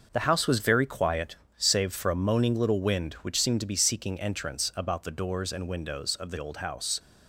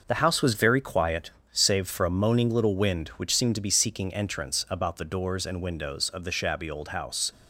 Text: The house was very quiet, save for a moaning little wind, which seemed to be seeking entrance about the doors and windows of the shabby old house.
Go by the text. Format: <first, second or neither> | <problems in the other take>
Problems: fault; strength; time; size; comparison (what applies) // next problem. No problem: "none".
second | starts louder than the rest; until 1.1 s; 6 dB; noticeable in the second // skips "shabby"; at 6.3 s